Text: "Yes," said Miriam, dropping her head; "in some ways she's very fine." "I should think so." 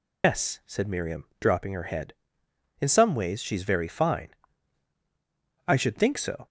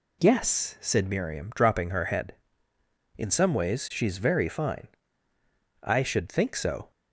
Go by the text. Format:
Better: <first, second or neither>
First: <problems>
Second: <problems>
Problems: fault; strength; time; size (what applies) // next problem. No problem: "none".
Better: second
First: loses the start of "Yes"; at 0.2 s; 140 ms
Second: none